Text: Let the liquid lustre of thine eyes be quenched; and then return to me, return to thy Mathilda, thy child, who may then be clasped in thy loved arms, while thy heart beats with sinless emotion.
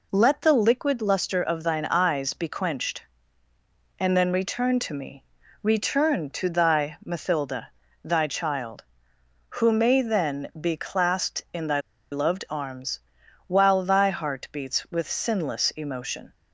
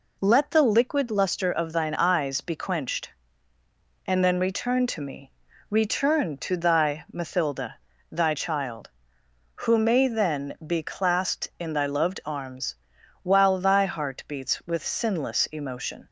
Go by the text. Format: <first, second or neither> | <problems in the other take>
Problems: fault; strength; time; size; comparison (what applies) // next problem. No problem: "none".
second | pauses between "thy" and "loved"; slight; at 11.8 s; 0.30 s long